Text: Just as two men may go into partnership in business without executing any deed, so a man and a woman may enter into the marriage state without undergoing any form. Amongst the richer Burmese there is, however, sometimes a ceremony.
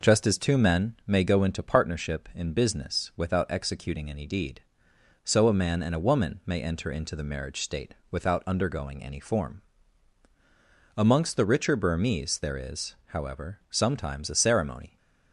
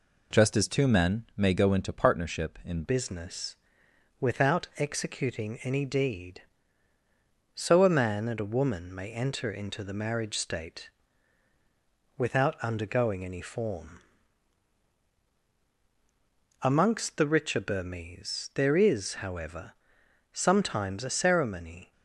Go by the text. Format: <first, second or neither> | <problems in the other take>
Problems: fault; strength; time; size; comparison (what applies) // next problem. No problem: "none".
first | changes voice at "business"; from 2.8 s on; 19.1 s long // pauses between "business" and "without"; noticeable; at 3.5 s; 0.64 s long // pauses between "state" and "without"; strong; at 10.8 s; 1.2 s long; slight in the first